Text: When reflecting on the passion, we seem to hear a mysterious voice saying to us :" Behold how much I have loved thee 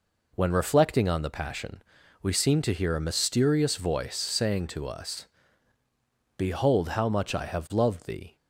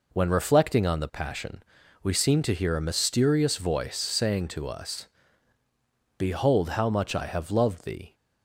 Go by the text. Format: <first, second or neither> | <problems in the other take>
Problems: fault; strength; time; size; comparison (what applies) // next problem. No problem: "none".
neither | none